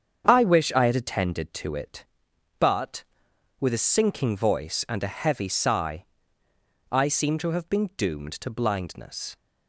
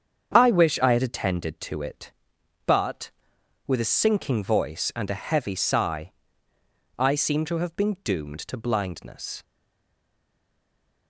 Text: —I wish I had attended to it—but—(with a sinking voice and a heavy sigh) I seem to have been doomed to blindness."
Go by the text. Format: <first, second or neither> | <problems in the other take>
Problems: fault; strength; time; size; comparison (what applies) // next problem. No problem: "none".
first | starts louder than the rest; strong; until 1.3 s; 7.5 dB; strong in the first // stays silent after the last word; noticeable; from 9.4 s on; 1.6 s long